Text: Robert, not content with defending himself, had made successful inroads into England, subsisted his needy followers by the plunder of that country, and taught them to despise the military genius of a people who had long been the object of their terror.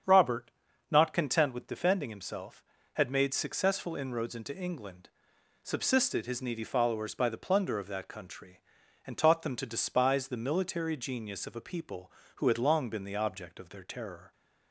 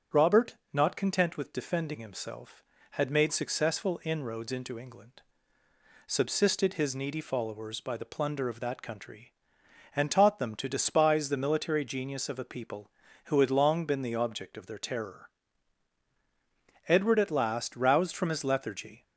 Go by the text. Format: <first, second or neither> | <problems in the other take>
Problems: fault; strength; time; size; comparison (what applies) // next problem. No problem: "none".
first | starts louder than the rest; strong; until 1.2 s; 7.5 dB; strong in the first // goes on to say "Edward at last roused from his lethargy"; strong; from 16.8 s on; 2.1 s long